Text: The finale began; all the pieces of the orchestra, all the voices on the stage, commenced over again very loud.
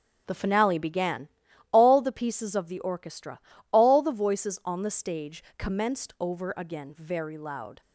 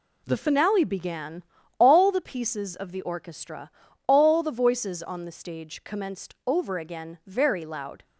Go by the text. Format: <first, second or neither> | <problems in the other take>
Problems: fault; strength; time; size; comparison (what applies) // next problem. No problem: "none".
second | starts louder than the rest; strong; until 1.4 s; 8 dB